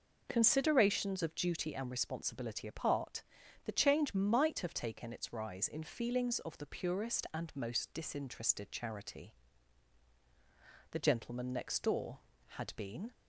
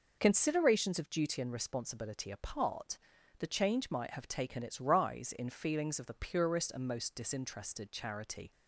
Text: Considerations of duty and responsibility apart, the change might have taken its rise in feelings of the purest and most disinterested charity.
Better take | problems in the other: second | goes on to say "The gentleman next door had been"; strong; from 10.9 s on; 2.2 s long

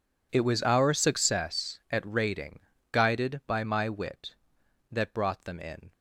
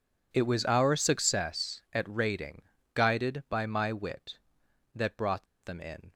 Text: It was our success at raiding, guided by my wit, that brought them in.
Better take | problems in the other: first | pauses between "brought" and "them"; slight; at 5.4 s; 0.20 s long

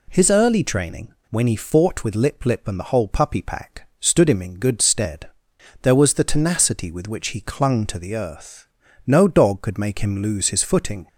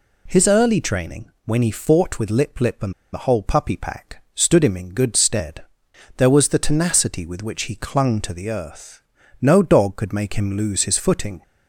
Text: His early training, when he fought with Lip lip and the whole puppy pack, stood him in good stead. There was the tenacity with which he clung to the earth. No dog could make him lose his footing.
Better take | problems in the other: first | pauses between "and" and "the"; slight; at 2.9 s; 0.20 s long

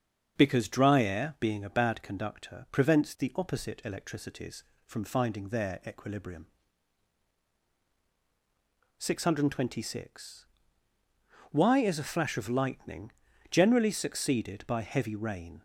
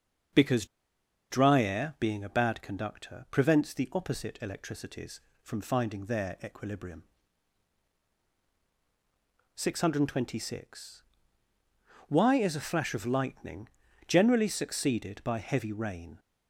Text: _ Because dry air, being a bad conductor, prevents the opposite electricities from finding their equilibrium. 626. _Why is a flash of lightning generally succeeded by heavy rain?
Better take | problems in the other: first | starts louder than the rest; until 2.0 s; 7 dB; also in the first // pauses between "Because" and "dry"; noticeable; at 0.6 s; 0.65 s long // pauses between "lightning" and "generally"; at 13.6 s; 0.40 s long; also in the first

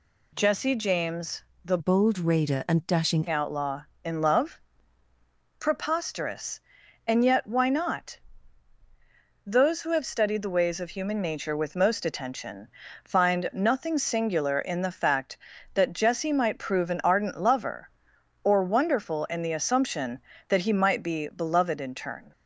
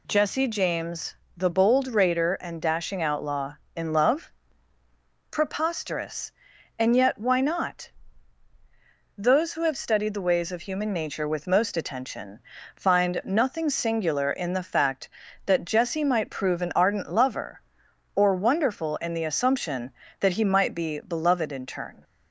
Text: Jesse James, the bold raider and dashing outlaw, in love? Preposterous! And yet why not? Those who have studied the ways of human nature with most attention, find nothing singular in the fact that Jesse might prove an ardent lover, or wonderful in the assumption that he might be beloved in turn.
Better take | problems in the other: second | changes voice from "bold" to "dashing"; from 1.7 to 3.2 s; 1.5 s long

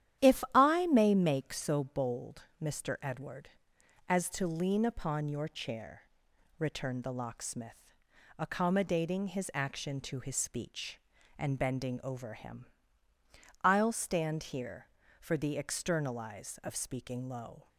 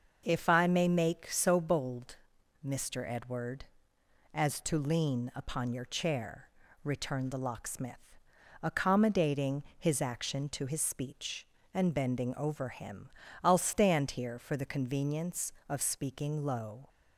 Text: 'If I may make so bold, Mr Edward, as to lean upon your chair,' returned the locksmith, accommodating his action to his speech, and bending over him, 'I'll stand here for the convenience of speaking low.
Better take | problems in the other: second | starts louder than the rest; strong; until 1.3 s; 11 dB; noticeable in the second // says "externalize" for "convenience"; at 15.5 s

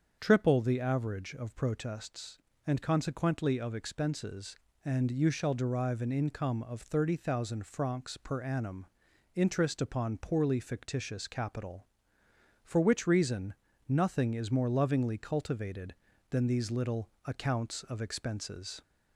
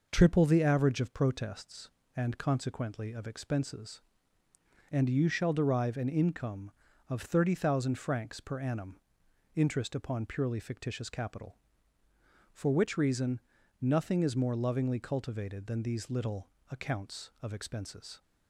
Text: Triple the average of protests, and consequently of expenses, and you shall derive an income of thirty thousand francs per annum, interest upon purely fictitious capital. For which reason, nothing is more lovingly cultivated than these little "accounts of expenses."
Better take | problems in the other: second | starts louder than the rest; strong; until 1.2 s; 7 dB // says "poorly" for "purely"; at 10.1 s // pauses between "little" and "accounts"; slight; at 17.0 s; 0.16 s long; slight in the second

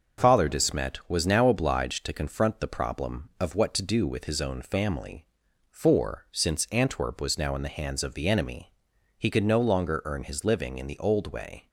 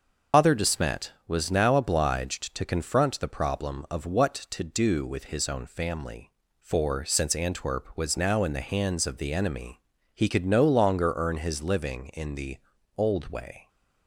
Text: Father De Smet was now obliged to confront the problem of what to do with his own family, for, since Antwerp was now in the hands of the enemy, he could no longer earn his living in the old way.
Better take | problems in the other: first | loses the start of "Father"; at 0.3 s; 165 ms // starts louder than the rest; noticeable; until 1.5 s; 6 dB; also in the first // pauses between "the" and "old"; at 12.5 s; 0.40 s long

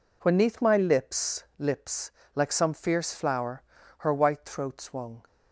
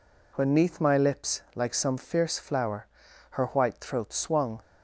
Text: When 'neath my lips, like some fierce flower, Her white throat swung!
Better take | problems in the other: second | says "lips" twice; at 1.5 s

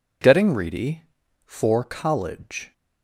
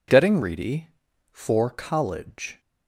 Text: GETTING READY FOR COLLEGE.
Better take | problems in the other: neither | none

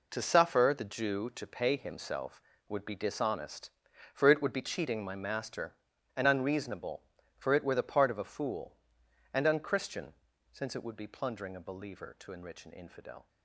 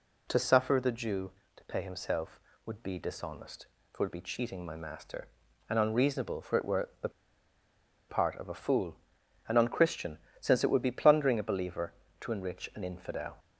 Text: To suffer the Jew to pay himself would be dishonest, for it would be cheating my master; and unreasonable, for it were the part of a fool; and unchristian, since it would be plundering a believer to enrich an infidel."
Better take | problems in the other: first | pauses between "the" and "part"; at 7.0 s; 0.99 s long

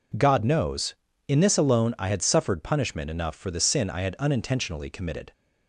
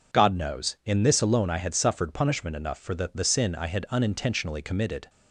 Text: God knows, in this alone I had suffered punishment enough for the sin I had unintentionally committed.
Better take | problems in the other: first | says "the" twice; at 3.1 s

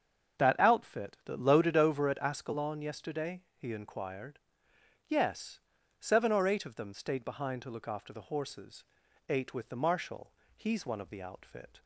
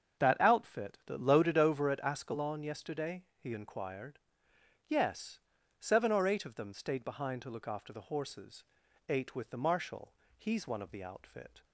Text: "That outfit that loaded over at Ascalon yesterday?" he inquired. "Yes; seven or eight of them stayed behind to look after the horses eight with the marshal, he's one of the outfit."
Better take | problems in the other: neither | starts louder than the rest; the same in both // pauses between "horses" and "eight"; noticeable; the same in both

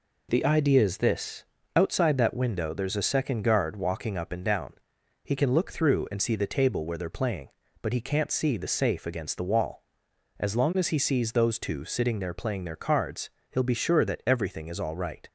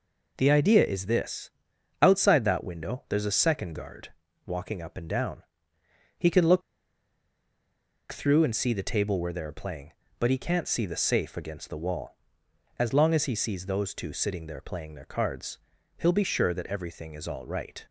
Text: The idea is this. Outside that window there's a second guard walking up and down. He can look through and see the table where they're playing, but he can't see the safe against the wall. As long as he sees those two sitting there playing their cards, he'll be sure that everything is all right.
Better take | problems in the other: first | pauses between "guard" and "walking"; at 4.0 s; 0.38 s long // pauses between "look" and "through"; strong; at 6.6 s; 1.5 s long

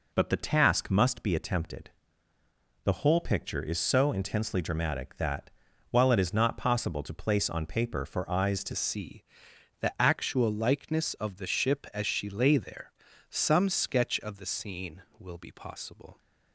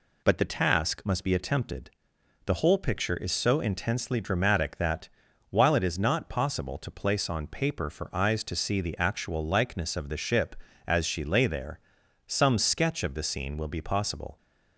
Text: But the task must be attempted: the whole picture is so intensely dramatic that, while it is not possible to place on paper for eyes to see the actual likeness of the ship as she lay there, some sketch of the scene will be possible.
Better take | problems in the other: second | changes voice at "see"; from 8.7 s on; 7.4 s long // pauses between "see" and "the"; noticeable; at 9.2 s; 0.58 s long

